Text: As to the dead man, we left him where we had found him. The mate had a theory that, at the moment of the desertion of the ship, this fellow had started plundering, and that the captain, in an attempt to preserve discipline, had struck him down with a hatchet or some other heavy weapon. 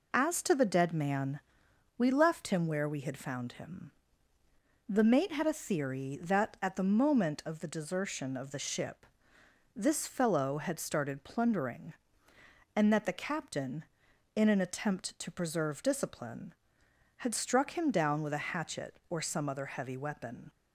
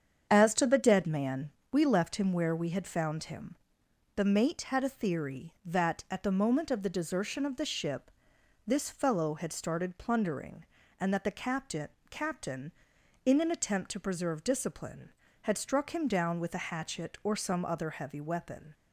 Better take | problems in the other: first | starts louder than the rest; strong; until 1.3 s; 8 dB // says "captain" twice; at 12.0 s

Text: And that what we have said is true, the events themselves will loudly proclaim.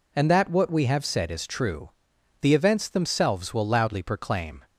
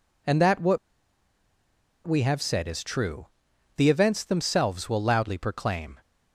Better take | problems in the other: first | pauses between "what" and "we"; strong; at 0.7 s; 1.2 s long

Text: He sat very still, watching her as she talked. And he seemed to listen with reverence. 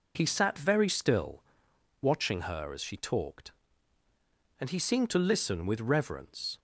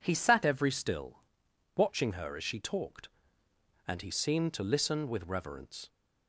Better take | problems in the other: first | says "every" for "very"; at 0.4 s

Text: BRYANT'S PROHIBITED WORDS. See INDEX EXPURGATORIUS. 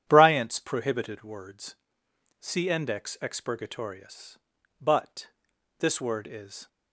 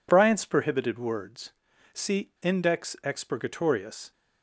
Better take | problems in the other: second | goes on to say "BUT This word is"; strong; from 4.8 s on; 1.8 s long

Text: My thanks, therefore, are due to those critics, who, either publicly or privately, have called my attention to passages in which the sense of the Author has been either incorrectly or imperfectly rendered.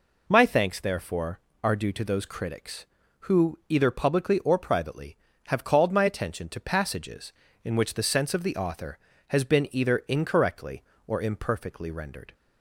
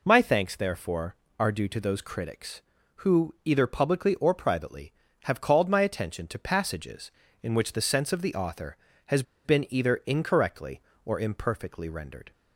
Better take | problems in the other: first | pauses between "has" and "been"; slight; at 9.2 s; 0.22 s long

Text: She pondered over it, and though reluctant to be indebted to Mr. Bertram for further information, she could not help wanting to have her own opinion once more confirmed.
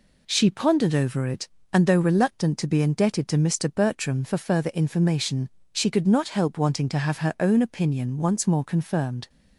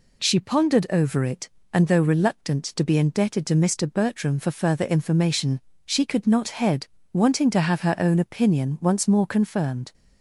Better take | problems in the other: first | says "head" for "help"; at 6.4 s

